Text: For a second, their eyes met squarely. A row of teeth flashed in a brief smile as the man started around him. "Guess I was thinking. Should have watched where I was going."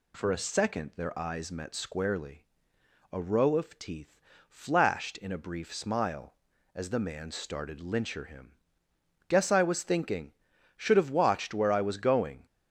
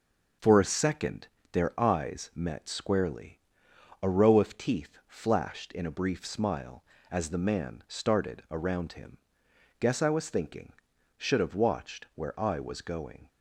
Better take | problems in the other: second | pauses between "teeth" and "flashed"; slight; at 4.1 s; 0.30 s long // says "lyncher" for "around"; at 7.7 s

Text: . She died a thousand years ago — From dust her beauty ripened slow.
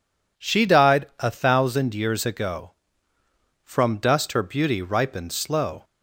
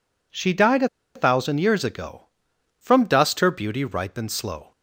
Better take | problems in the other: first | pauses between "a" and "thousand"; slight; at 0.8 s; 0.28 s long

